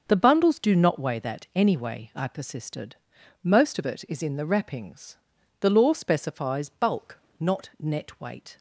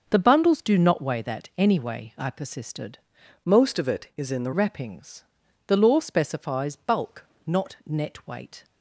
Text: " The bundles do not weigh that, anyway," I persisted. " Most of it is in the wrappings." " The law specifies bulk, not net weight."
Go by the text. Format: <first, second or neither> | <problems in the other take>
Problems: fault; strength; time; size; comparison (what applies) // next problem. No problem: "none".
first | changes voice from "Most" to "the"; from 3.4 to 4.5 s; 1.1 s long